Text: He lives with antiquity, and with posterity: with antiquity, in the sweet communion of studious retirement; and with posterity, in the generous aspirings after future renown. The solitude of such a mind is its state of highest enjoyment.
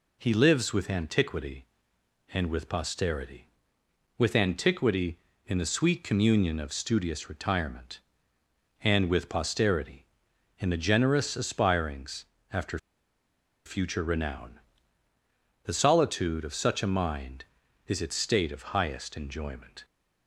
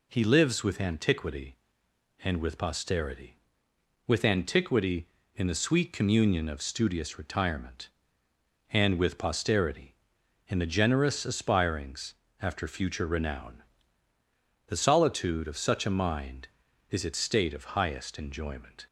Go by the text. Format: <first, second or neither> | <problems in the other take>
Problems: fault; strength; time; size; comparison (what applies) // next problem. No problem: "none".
second | pauses between "aspirings" and "after"; slight; at 12.2 s; 0.26 s long; slight in the second // pauses between "after" and "future"; noticeable; at 12.7 s; 0.88 s long